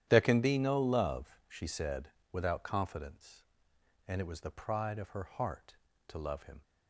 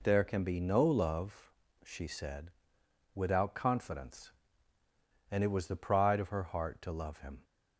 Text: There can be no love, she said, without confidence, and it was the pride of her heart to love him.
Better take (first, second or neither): second